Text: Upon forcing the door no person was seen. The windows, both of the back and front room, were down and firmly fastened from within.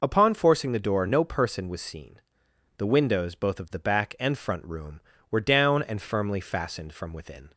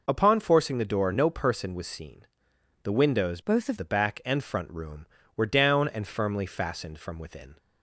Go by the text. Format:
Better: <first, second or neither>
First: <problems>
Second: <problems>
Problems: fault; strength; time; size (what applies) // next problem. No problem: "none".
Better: first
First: none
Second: changes voice from "both" to "of"; from 3.4 to 3.7 s; 0.3 s long